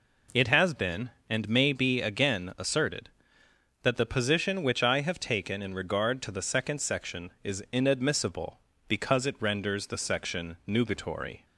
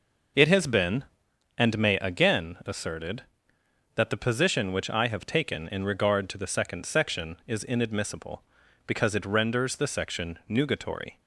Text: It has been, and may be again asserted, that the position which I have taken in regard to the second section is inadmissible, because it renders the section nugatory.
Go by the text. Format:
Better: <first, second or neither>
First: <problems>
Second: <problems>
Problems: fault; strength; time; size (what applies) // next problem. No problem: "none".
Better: first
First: none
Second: skips "be"; at 1.9 s